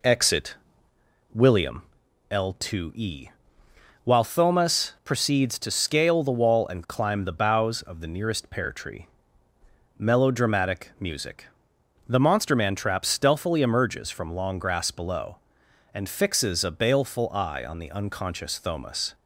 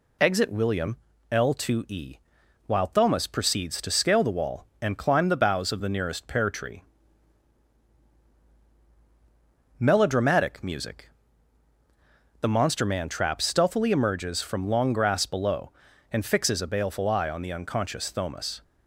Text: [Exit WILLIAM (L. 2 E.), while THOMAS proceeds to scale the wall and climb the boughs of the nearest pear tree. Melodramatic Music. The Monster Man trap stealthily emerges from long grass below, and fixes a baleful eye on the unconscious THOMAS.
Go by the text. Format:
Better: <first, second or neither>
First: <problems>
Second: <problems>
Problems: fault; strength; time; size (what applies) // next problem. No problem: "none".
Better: second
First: starts louder than the rest; slight; until 1.8 s; 3.5 dB // pauses between "Exit" and "WILLIAM"; noticeable; at 0.5 s; 0.80 s long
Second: none